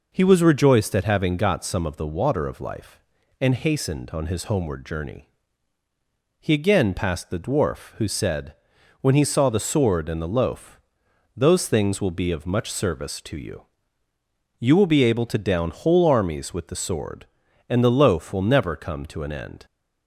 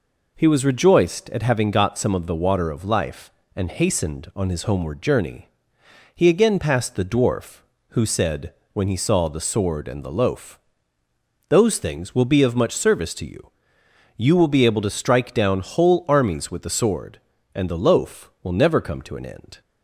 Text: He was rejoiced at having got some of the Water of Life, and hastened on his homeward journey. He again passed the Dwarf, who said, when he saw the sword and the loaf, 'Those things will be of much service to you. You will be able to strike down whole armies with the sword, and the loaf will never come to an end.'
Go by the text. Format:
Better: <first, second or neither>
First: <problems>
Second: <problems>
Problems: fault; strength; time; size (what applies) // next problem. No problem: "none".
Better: second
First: skips "strike"; at 15.3 s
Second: none